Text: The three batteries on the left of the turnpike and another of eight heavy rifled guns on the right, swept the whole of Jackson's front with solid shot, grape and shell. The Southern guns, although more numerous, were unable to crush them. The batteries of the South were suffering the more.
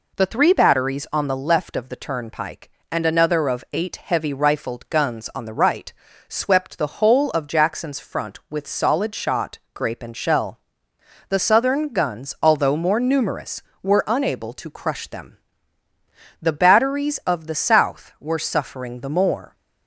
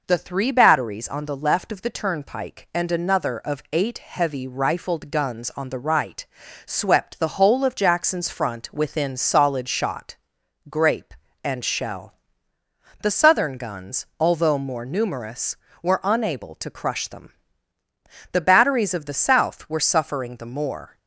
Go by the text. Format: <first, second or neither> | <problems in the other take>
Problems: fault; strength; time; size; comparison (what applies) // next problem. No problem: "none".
first | says "within" for "with"; at 8.7 s